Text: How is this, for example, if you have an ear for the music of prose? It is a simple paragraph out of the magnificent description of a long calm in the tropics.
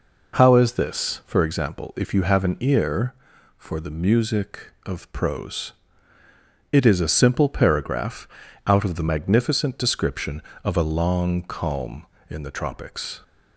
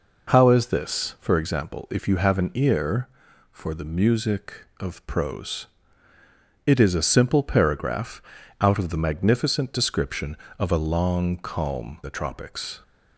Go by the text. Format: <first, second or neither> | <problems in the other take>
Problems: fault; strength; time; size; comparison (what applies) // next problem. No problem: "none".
first | pauses between "paragraph" and "out"; at 8.2 s; 0.40 s long; also in the first // skips "in"; at 12.0 s